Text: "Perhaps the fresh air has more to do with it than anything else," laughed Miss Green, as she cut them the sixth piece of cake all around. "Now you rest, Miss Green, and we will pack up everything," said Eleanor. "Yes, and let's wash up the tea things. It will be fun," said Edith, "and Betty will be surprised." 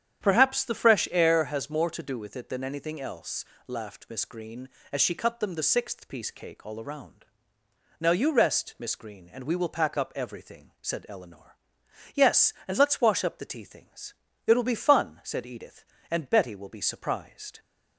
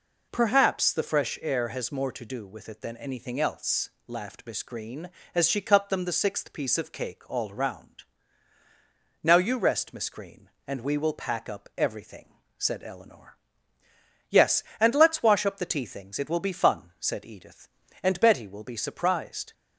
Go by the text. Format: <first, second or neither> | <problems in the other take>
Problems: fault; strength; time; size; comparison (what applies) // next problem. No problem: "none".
second | starts louder than the rest; strong; until 1.2 s; 9 dB // skips "of"; at 6.3 s